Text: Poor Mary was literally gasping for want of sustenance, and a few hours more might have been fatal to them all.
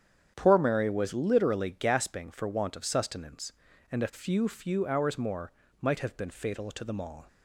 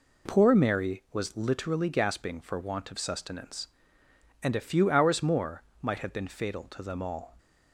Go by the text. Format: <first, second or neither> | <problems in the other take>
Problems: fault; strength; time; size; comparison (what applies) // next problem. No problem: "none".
second | starts louder than the rest; strong; until 1.3 s; 8.5 dB // says "few" twice; at 4.4 s // pauses between "more" and "might"; slight; at 5.5 s; 0.30 s long; slight in the second